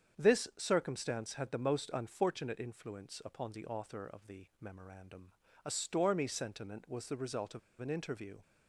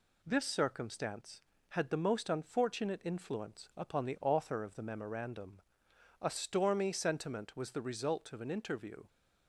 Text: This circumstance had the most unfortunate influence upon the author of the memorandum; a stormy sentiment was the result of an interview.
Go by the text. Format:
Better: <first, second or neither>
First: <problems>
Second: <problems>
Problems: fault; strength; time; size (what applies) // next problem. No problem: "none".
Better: second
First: starts louder than the rest; strong; until 1.2 s; 7.5 dB // pauses between "the" and "memorandum"; slight; at 4.4 s; 0.16 s long // pauses between "of" and "an"; slight; at 7.5 s; 0.21 s long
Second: none